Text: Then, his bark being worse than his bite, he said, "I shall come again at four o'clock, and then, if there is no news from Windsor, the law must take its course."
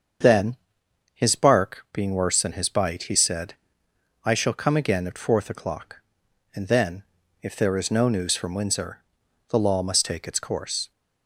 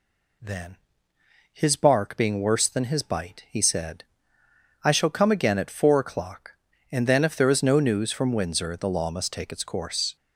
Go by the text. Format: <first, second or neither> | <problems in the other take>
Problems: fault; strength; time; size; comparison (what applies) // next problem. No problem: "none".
second | starts louder than the rest; until 1.8 s; 7 dB // says "fourth" for "four"; at 5.1 s